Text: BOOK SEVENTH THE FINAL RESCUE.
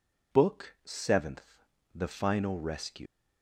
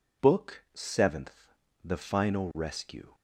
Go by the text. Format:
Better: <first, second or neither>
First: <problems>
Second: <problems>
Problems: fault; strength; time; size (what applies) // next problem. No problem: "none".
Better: second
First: pauses between "SEVENTH" and "THE"; slight; at 1.6 s; 0.28 s long // leaves "RESCUE" unfinished; at 3.0 s; 150 ms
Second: pauses between "SEVENTH" and "THE"; slight; at 1.5 s; 0.28 s long